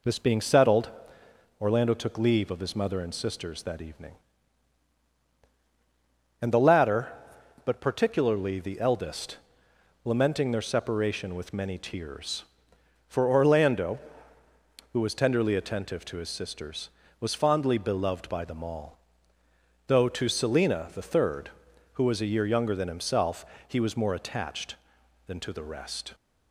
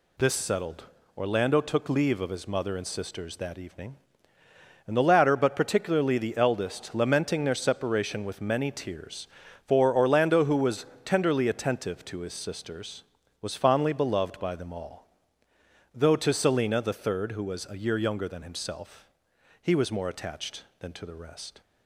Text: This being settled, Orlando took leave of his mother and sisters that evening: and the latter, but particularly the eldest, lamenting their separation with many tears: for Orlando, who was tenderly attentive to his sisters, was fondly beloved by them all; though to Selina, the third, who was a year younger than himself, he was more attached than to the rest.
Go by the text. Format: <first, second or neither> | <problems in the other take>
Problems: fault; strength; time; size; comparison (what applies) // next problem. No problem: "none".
first | skips "being"; at 0.3 s // pauses between "was" and "tenderly"; slight; at 10.8 s; 0.18 s long